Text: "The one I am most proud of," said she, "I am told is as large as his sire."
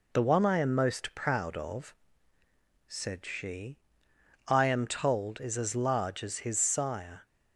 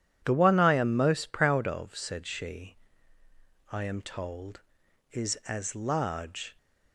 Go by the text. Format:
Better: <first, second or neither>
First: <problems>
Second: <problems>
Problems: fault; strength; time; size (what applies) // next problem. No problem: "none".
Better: first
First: none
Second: stops before "as his sire"; at 6.5 s